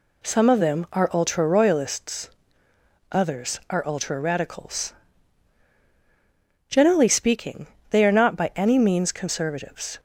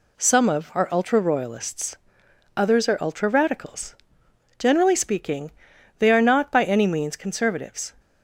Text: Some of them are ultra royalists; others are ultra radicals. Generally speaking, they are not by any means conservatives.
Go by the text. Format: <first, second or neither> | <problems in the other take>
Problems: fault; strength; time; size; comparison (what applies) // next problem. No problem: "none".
first | skips "them"; at 0.7 s